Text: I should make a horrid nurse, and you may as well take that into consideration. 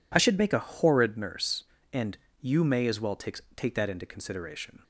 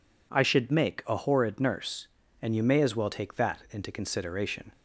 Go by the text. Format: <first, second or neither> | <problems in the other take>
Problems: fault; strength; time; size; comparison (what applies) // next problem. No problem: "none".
second | pauses between "and" and "you"; slight; at 2.1 s; 0.24 s long // says "take" twice; at 3.5 s